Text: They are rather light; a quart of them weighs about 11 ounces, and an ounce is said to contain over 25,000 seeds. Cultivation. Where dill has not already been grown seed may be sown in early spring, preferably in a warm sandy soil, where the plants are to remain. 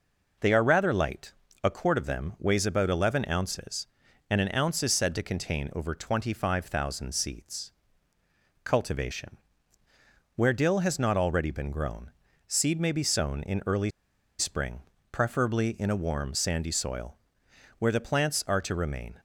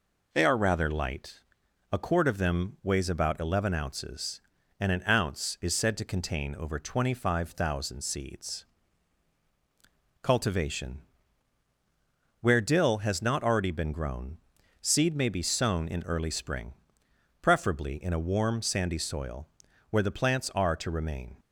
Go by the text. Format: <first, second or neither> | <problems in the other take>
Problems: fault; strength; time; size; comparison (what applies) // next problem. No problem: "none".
second | pauses between "grown" and "seed"; slight; at 12.1 s; 0.34 s long; also in the second // pauses between "early" and "spring"; noticeable; at 13.8 s; 0.49 s long